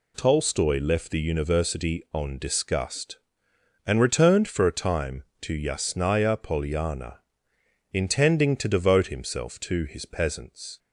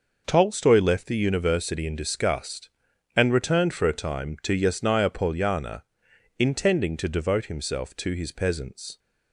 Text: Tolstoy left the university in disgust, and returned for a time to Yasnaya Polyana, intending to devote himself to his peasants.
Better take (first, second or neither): second